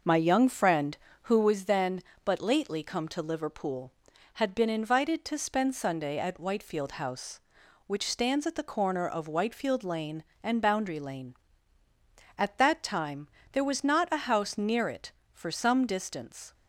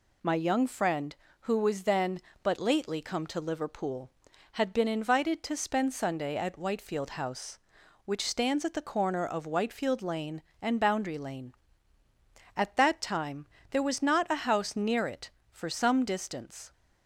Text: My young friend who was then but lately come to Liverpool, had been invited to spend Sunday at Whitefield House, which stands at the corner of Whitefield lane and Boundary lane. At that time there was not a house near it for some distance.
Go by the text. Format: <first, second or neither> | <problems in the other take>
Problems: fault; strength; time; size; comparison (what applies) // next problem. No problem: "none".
second | starts louder than the rest; noticeable; until 1.6 s; 5.5 dB // pauses between "time" and "there"; slight; at 13.2 s; 0.24 s long; slight in the second